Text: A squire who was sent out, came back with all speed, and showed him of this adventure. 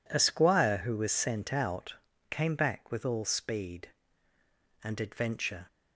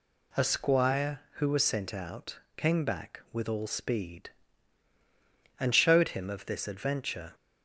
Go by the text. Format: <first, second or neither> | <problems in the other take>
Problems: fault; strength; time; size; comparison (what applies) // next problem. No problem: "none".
second | skips "showed him of this"; at 5.0 s